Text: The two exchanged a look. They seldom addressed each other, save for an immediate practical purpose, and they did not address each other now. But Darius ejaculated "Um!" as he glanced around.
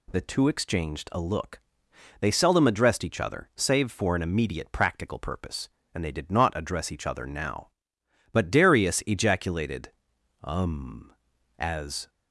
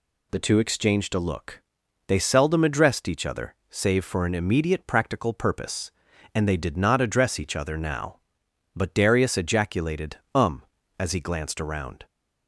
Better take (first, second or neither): second